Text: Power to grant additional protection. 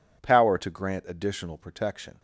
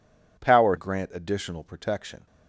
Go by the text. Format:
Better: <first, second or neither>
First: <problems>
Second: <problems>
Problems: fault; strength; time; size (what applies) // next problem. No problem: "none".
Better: first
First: none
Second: skips "to"; at 0.7 s